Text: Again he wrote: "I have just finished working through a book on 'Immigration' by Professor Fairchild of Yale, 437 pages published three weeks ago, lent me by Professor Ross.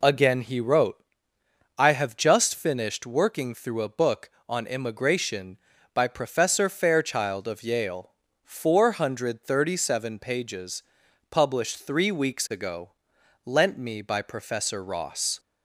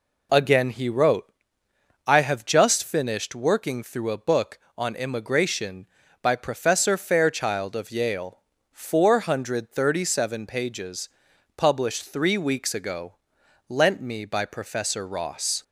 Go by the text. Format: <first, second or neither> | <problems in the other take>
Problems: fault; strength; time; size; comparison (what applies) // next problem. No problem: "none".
neither | pauses between "pages" and "published"; noticeable; the same in both